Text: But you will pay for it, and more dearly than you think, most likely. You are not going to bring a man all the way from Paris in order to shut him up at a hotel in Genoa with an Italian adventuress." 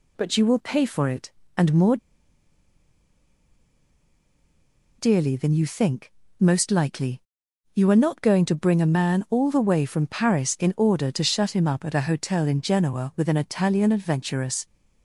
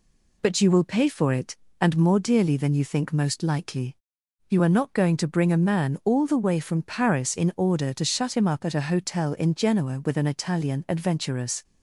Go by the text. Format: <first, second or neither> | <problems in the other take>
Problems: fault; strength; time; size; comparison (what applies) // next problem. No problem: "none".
second | pauses between "more" and "dearly"; strong; at 1.9 s; 3.0 s long